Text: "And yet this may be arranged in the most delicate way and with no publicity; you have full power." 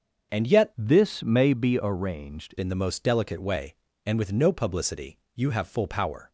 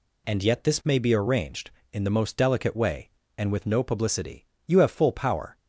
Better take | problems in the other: second | starts louder than the rest; until 1.4 s; 6.5 dB // changes voice from "this" to "arranged"; from 0.7 to 2.5 s; 1.8 s long

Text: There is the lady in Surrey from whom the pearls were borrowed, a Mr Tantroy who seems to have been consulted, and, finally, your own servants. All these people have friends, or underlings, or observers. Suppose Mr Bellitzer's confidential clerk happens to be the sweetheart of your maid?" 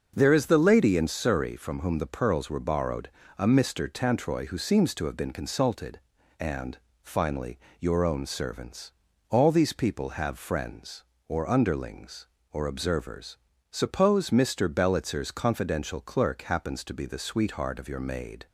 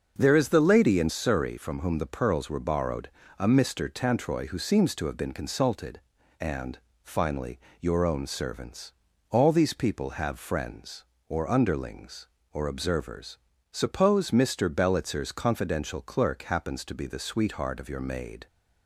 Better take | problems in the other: neither | starts louder than the rest; noticeable; the same in both

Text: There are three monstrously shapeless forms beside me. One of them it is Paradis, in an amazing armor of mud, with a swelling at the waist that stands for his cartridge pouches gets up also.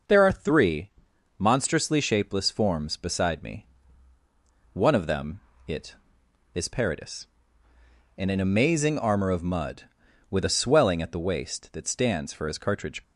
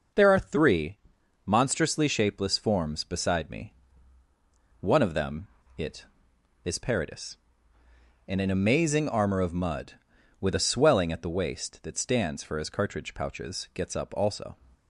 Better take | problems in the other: second | pauses between "three" and "monstrously"; noticeable; at 0.9 s; 0.48 s long; noticeable in the second // pauses between "them" and "it"; slight; at 5.3 s; 0.28 s long; slight in the second // stops before "pouches gets up also"; at 13.0 s

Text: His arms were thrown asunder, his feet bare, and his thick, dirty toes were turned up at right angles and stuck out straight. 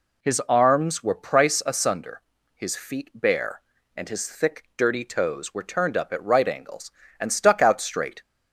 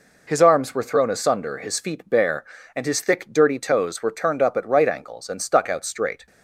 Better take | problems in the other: second | says "price" for "thrown"; at 1.1 s

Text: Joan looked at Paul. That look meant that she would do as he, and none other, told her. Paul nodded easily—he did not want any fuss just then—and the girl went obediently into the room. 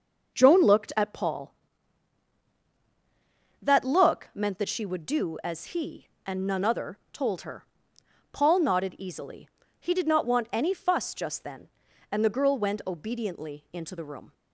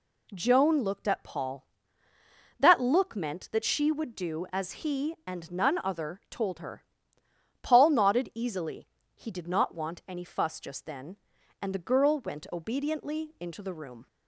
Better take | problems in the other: neither | none

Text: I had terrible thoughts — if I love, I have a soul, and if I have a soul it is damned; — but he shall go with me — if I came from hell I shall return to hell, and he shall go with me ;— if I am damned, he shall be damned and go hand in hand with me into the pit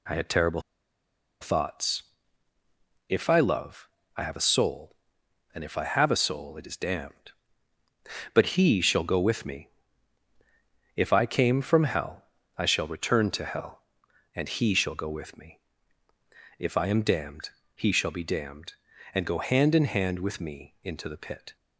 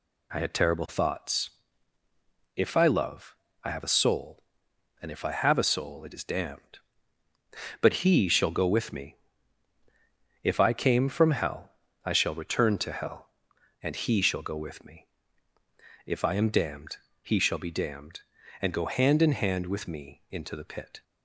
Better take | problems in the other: second | pauses between "terrible" and "thoughts"; noticeable; at 0.6 s; 0.80 s long // pauses between "hell" and "I"; slight; at 12.2 s; 0.34 s long; slight in the second

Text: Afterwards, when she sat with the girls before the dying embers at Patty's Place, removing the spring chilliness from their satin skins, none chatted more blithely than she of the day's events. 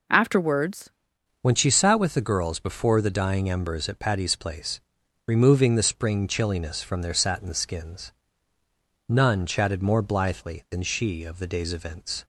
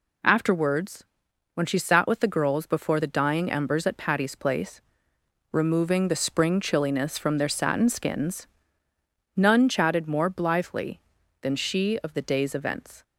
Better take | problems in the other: second | changes voice at "when"; from 1.4 s on; 10.8 s long

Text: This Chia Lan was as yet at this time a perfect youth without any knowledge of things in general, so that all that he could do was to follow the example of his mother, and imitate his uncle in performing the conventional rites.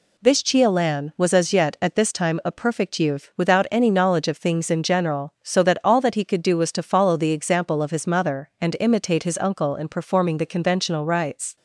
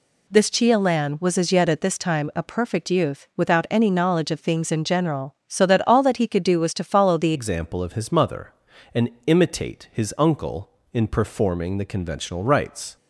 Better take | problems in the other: first | changes voice at "example"; from 7.3 s on; 5.6 s long // pauses between "and" and "imitate"; slight; at 9.0 s; 0.16 s long

